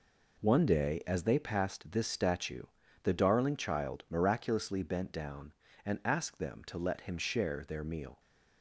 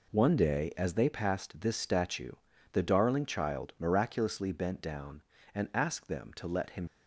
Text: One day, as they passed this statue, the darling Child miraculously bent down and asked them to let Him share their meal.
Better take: first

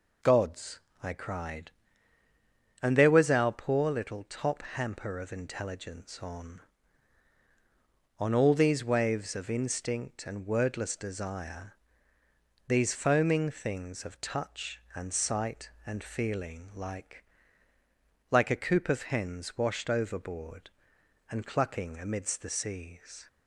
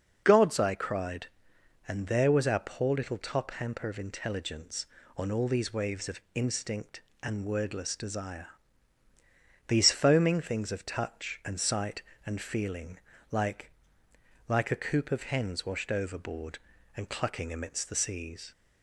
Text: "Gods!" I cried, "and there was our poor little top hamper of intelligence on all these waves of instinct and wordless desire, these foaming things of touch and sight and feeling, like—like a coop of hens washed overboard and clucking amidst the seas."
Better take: second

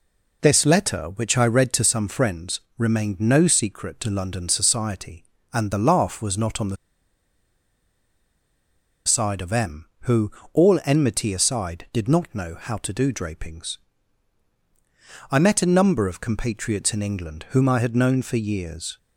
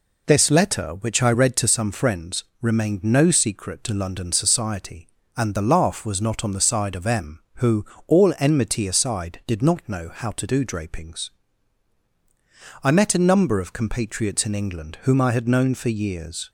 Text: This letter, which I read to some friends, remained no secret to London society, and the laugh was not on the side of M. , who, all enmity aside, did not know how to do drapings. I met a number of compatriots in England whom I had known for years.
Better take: second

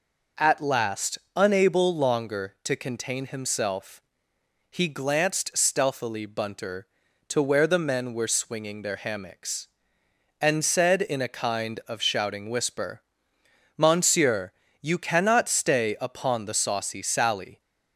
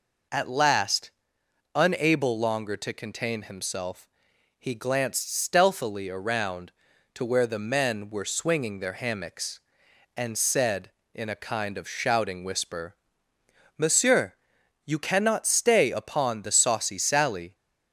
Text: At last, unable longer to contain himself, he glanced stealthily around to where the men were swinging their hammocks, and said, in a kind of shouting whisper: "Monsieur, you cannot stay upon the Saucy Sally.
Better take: second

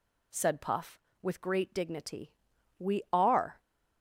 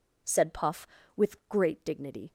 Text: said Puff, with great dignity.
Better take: second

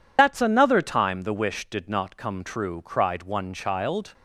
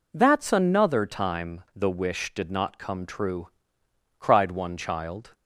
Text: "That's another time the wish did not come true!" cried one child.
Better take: second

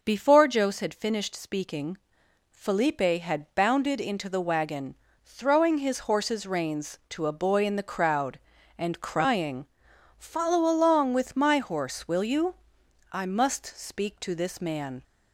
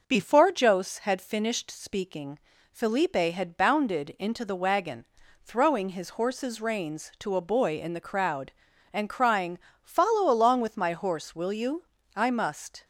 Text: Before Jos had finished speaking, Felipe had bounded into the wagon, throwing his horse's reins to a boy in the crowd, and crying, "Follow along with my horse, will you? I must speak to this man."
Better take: first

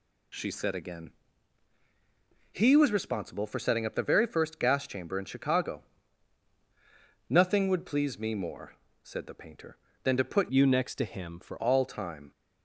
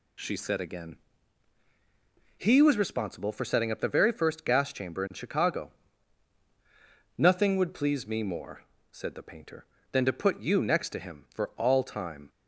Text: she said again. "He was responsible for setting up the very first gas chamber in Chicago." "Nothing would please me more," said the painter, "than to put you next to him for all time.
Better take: second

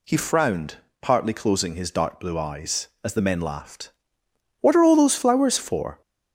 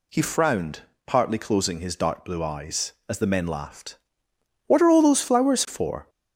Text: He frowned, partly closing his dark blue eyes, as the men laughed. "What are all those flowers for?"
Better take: neither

